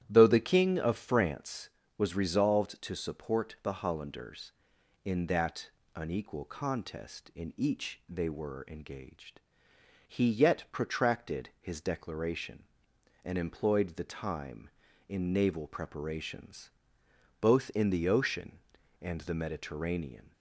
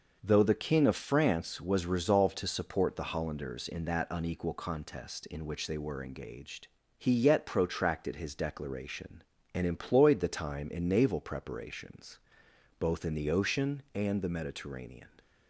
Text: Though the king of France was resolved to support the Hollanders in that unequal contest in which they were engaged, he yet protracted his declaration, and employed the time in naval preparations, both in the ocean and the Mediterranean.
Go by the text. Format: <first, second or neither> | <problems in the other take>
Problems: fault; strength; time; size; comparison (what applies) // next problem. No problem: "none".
second | starts louder than the rest; strong; until 1.0 s; 11.5 dB // pauses between "that" and "unequal"; slight; at 5.7 s; 0.24 s long // says "each" for "which"; at 7.5 s